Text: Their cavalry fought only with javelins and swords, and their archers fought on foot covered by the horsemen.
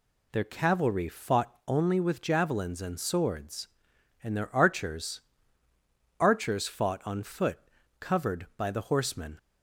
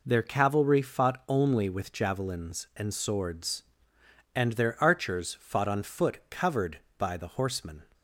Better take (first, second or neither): second